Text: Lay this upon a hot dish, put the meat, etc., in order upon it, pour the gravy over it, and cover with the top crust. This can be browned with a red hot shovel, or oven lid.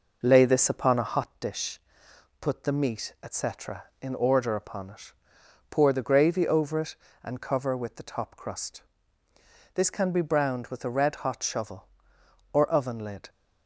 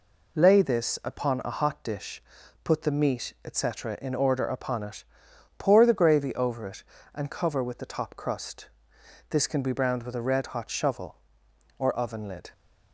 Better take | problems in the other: second | starts louder than the rest; noticeable; until 1.3 s; 5 dB

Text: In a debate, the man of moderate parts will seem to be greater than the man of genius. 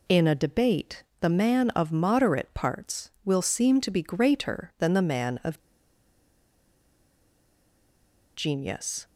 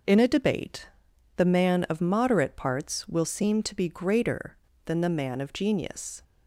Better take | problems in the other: second | pauses between "of" and "genius"; strong; at 5.5 s; 2.7 s long

